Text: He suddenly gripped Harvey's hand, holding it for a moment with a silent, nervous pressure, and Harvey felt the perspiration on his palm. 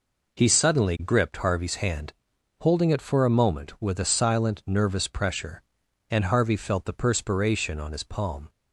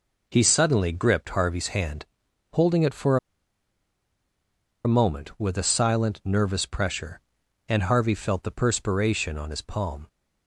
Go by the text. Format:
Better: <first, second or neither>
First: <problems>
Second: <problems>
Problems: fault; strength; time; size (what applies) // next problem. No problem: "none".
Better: first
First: none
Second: pauses between "for" and "a"; strong; at 3.1 s; 1.6 s long